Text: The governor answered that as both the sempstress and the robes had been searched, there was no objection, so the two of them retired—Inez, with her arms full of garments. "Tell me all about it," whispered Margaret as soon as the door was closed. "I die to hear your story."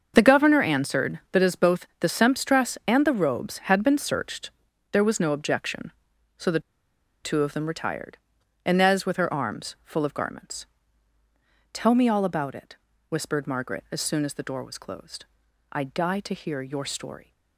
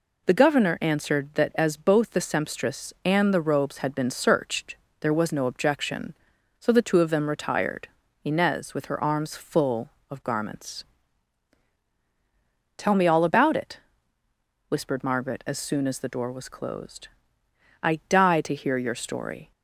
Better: second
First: starts louder than the rest; until 1.1 s; 6.5 dB // pauses between "the" and "two"; noticeable; at 6.6 s; 0.62 s long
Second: none

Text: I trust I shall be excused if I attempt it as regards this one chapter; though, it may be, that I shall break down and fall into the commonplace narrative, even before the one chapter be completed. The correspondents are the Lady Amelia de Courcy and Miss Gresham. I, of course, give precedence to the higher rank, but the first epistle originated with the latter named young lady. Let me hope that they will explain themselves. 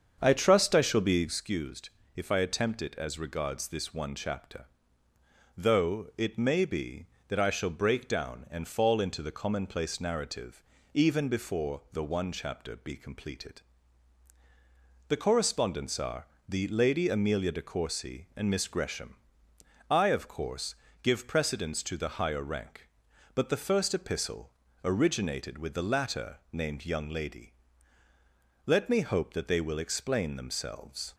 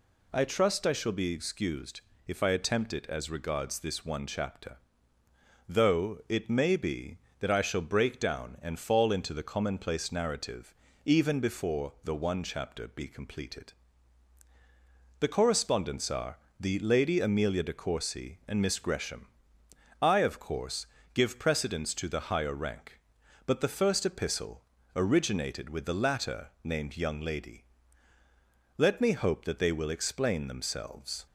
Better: second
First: starts louder than the rest; strong; until 1.4 s; 7 dB // pauses between "excused" and "if"; slight; at 1.9 s; 0.26 s long // pauses between "are" and "the"; slight; at 16.2 s; 0.22 s long // pauses between "epistle" and "originated"; slight; at 24.5 s; 0.32 s long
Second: pauses between "excused" and "if"; slight; at 2.0 s; 0.26 s long // pauses between "are" and "the"; slight; at 16.3 s; 0.22 s long // pauses between "epistle" and "originated"; slight; at 24.6 s; 0.32 s long

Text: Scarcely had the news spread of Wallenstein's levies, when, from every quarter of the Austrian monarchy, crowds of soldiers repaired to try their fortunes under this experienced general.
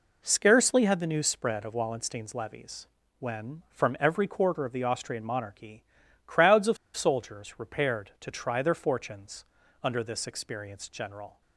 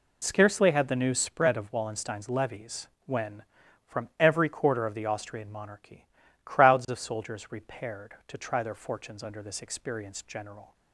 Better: second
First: pauses between "of" and "soldiers"; slight; at 6.7 s; 0.19 s long // pauses between "fortunes" and "under"; at 9.4 s; 0.40 s long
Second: none

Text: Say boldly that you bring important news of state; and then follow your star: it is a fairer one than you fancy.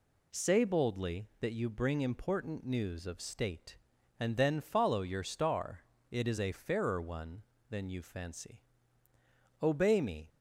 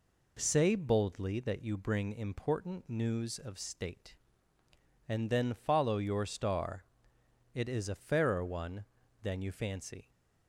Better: second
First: goes on to say "obey me"; noticeable; from 9.6 s on; 0.66 s long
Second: none

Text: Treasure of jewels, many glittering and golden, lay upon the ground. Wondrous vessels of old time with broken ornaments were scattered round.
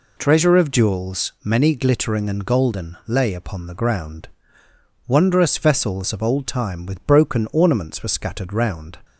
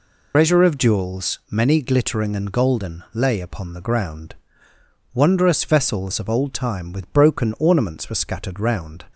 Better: first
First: none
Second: loses the start of "Treasure"; at 0.3 s; 95 ms

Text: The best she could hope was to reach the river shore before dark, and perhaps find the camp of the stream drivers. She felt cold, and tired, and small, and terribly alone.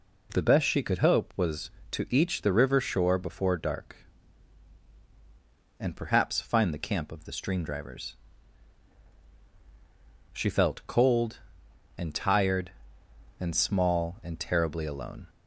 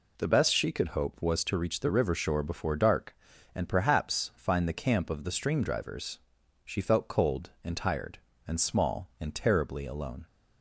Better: second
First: says "each" for "reach"; at 2.0 s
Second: none

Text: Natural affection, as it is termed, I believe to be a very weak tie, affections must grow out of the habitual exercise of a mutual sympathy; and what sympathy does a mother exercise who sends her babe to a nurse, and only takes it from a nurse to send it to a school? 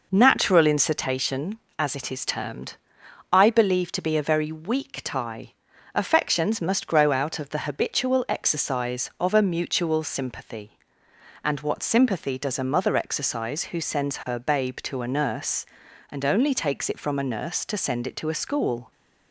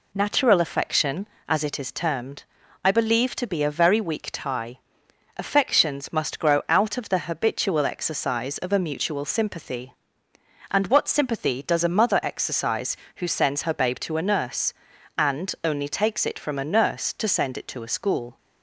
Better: second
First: says "incitation" for "affection"; at 0.6 s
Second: none

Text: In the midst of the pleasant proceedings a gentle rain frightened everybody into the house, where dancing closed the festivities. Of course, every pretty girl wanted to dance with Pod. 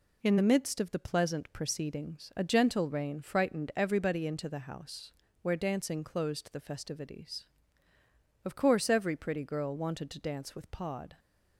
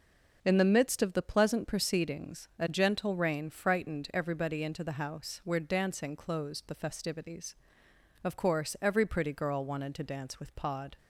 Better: neither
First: none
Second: none

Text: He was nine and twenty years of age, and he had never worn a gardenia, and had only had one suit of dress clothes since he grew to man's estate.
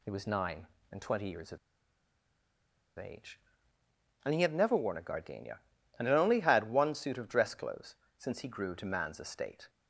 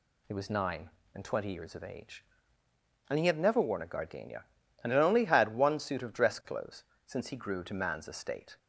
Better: second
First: pauses between "of" and "age"; strong; at 1.5 s; 1.4 s long // pauses between "clothes" and "since"; slight; at 7.9 s; 0.22 s long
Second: pauses between "clothes" and "since"; slight; at 6.8 s; 0.22 s long

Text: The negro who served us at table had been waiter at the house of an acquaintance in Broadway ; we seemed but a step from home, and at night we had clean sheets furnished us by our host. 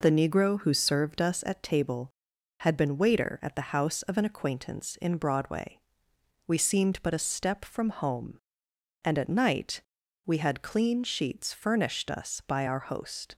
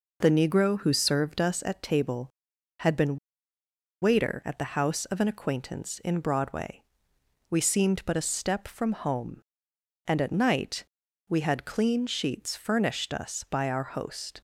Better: first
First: pauses between "night" and "we"; at 9.8 s; 0.44 s long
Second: pauses between "been" and "waiter"; noticeable; at 3.1 s; 0.84 s long // pauses between "night" and "we"; at 10.8 s; 0.44 s long

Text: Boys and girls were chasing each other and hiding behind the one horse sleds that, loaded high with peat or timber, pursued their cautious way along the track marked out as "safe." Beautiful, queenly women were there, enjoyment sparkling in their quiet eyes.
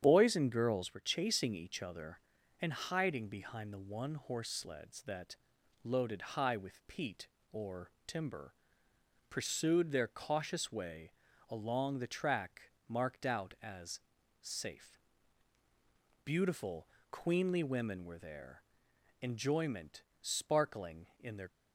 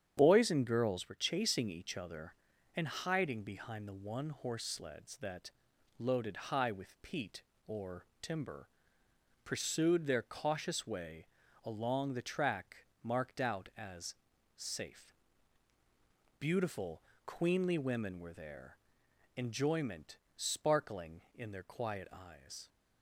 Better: second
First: starts louder than the rest; strong; until 1.0 s; 8.5 dB // pauses between "loaded" and "high"; slight; at 6.1 s; 0.16 s long // pauses between "or" and "timber"; slight; at 7.8 s; 0.16 s long // pauses between "way" and "along"; at 11.1 s; 0.38 s long // pauses between "track" and "marked"; slight; at 12.6 s; 0.22 s long // pauses between "as" and "safe"; at 14.0 s; 0.40 s long // pauses between "enjoyment" and "sparkling"; slight; at 20.0 s; 0.18 s long // stops before "quiet eyes"; at 21.4 s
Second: starts louder than the rest; strong; until 1.1 s; 8.5 dB // pauses between "loaded" and "high"; slight; at 6.3 s; 0.16 s long // pauses between "or" and "timber"; slight; at 8.0 s; 0.16 s long // pauses between "way" and "along"; at 11.2 s; 0.38 s long // pauses between "track" and "marked"; slight; at 12.7 s; 0.22 s long // pauses between "as" and "safe"; at 14.1 s; 0.40 s long // pauses between "enjoyment" and "sparkling"; slight; at 20.1 s; 0.18 s long

